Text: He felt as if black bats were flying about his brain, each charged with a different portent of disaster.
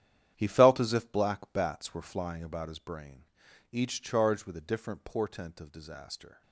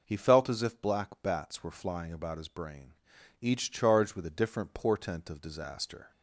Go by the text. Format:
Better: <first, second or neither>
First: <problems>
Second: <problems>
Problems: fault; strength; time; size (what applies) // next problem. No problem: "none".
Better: second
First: gets quieter; strong; throughout; 12 dB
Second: none